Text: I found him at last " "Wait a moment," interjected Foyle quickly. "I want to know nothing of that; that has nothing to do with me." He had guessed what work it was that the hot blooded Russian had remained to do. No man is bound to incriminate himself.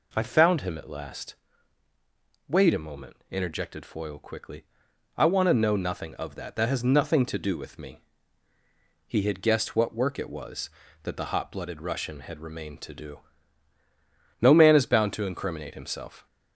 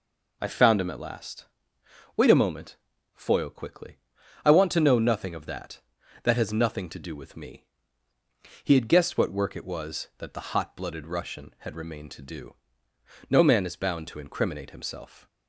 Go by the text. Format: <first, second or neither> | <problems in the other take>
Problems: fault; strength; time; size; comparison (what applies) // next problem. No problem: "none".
first | skips "interjected"; at 2.9 s